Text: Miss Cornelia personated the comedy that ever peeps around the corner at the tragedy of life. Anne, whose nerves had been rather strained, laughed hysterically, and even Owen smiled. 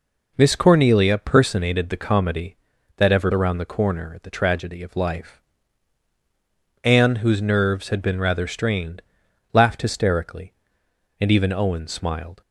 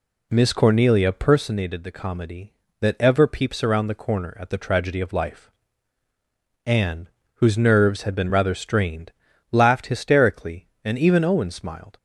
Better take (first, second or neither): second